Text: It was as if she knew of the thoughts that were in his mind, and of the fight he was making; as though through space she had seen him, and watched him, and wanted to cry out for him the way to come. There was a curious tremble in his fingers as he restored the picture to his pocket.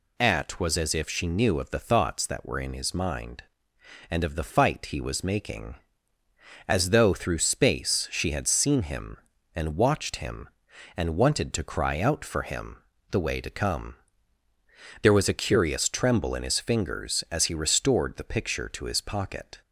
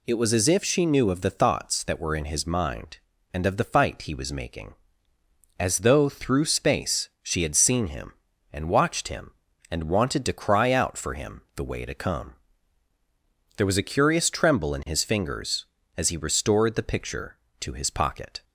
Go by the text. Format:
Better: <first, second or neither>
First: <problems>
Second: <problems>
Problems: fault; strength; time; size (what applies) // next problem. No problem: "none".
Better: second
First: says "At" for "It"; at 0.1 s // pauses between "him" and "the"; slight; at 12.7 s; 0.34 s long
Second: none